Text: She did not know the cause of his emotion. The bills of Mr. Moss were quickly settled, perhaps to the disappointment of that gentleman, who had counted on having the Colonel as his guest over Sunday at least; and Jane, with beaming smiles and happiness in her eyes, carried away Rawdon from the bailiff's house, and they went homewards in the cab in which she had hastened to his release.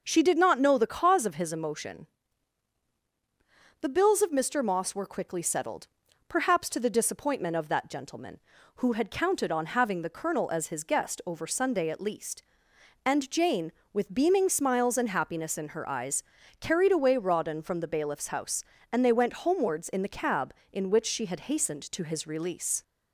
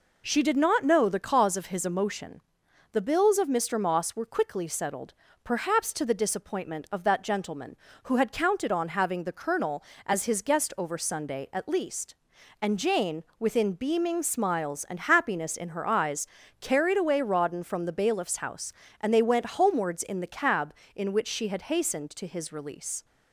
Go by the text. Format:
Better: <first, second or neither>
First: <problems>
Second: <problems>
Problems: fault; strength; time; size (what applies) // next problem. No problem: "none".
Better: first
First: none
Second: says "within" for "with"; at 13.3 s